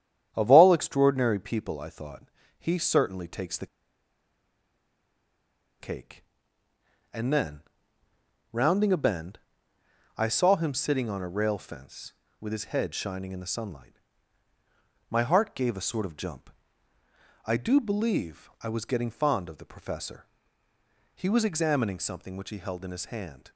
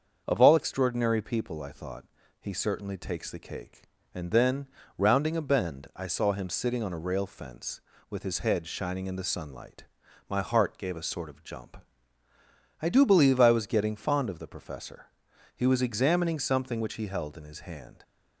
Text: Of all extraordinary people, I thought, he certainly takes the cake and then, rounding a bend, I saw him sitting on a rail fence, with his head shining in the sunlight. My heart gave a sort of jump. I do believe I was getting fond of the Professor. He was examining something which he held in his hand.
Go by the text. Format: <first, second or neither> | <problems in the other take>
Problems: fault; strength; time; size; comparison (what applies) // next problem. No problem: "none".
second | starts louder than the rest; strong; until 1.3 s; 9.5 dB; also in the second // pauses between "the" and "cake"; strong; at 3.6 s; 2.1 s long